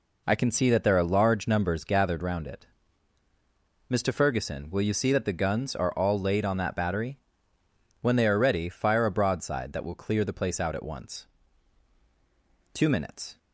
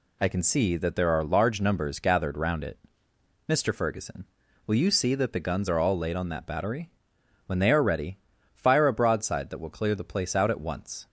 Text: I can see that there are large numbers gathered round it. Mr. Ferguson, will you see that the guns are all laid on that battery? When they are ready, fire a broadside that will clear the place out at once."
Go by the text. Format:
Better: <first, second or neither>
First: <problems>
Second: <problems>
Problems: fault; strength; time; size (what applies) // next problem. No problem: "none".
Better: second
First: goes on to say "Two minutes"; noticeable; from 12.7 s on; 0.66 s long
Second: none